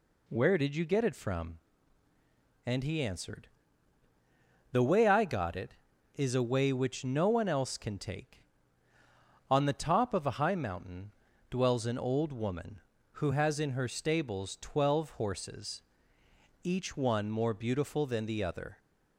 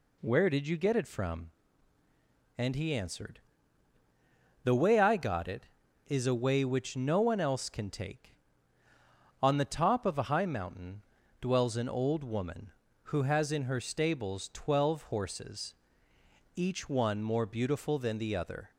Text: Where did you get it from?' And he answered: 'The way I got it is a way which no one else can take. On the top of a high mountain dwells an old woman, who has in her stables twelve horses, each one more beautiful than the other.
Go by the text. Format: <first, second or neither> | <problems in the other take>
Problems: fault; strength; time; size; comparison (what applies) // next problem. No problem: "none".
neither | pauses between "mountain" and "dwells"; slight; the same in both